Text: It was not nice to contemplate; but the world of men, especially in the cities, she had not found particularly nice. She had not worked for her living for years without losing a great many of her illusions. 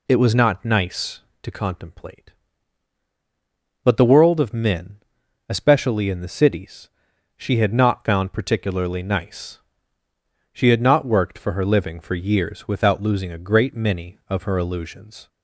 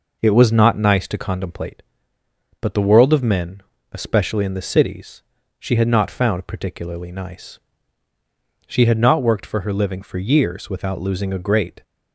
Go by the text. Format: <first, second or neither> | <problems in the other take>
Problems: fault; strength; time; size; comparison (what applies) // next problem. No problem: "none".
first | stops before "many of her illusions"; at 11.8 s